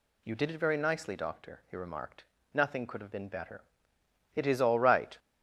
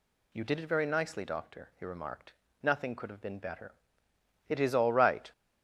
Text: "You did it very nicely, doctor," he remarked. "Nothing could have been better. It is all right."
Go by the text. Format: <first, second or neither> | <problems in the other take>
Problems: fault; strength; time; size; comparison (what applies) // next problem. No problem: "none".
neither | none